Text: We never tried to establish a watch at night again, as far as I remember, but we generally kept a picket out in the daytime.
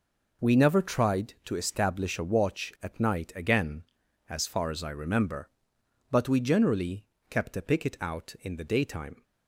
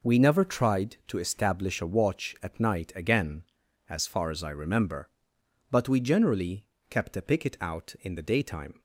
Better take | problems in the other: neither | pauses between "generally" and "kept"; slight; the same in both

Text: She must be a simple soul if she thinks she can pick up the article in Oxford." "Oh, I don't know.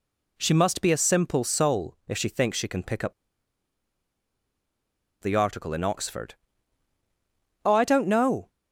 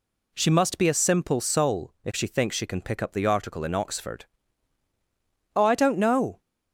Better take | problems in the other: second | pauses between "up" and "the"; strong; at 3.1 s; 2.0 s long

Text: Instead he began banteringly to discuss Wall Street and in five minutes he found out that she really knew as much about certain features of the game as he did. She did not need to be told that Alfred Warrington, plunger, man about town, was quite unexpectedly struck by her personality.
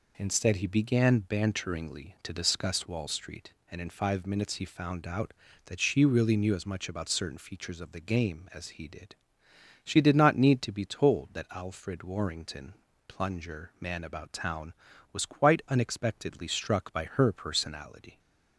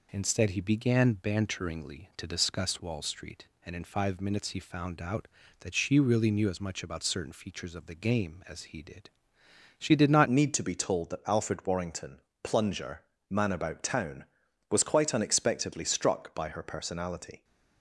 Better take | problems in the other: first | changes voice at "need"; from 10.2 s on; 7.2 s long

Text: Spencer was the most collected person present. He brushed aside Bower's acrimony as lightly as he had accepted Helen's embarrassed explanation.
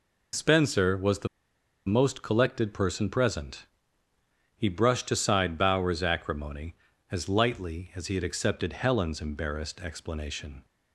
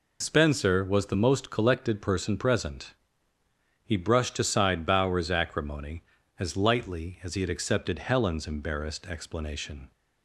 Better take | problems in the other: second | pauses between "the" and "most"; noticeable; at 1.2 s; 0.59 s long

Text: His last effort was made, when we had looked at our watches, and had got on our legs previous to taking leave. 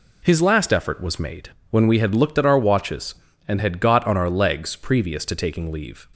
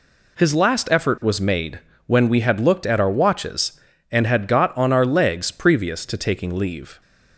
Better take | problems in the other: neither | none

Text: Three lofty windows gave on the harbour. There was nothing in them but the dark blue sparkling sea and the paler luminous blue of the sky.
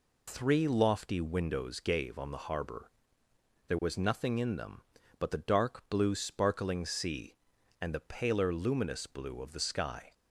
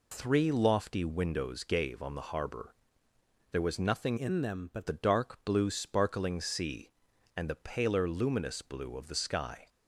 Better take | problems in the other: first | changes voice from "in" to "but"; from 4.1 to 4.8 s; 0.7 s long

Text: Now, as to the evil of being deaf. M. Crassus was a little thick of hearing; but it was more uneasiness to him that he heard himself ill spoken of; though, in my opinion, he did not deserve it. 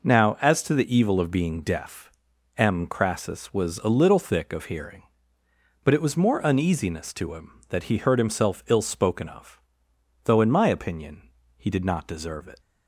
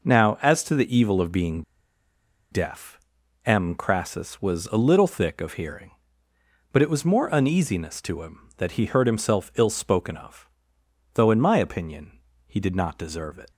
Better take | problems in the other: first | pauses between "being" and "deaf"; noticeable; at 1.6 s; 0.90 s long

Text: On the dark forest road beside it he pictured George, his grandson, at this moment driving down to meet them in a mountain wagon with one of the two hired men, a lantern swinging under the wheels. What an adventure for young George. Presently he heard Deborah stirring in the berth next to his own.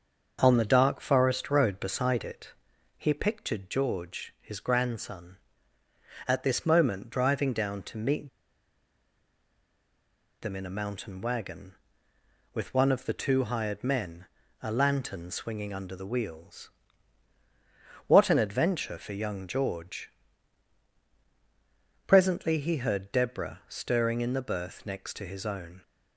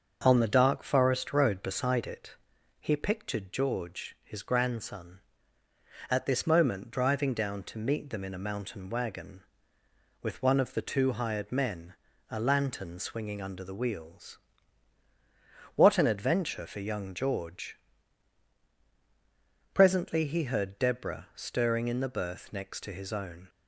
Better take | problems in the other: second | starts louder than the rest; until 1.4 s; 7 dB; also in the second // pauses between "it" and "he"; at 2.5 s; 0.44 s long; also in the second // pauses between "meet" and "them"; strong; at 8.2 s; 2.1 s long

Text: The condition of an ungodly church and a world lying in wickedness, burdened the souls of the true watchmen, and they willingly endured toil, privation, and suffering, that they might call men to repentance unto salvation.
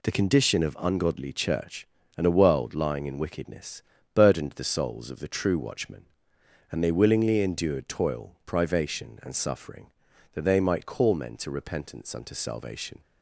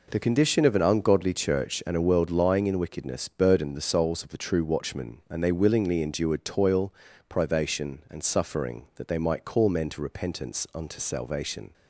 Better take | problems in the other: second | skips "an"; at 0.7 s

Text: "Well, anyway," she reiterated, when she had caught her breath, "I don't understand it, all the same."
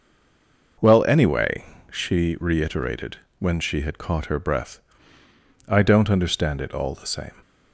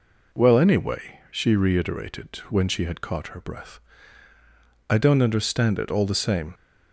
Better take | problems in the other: second | stays silent before the first word; slight; until 0.7 s; 0.7 s long

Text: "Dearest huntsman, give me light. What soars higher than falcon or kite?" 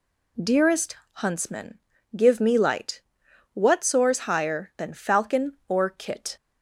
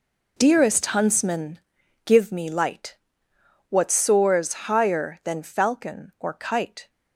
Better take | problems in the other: second | pauses between "Dearest" and "huntsman"; slight; at 0.9 s; 0.24 s long // says "kit" for "kite"; at 5.8 s

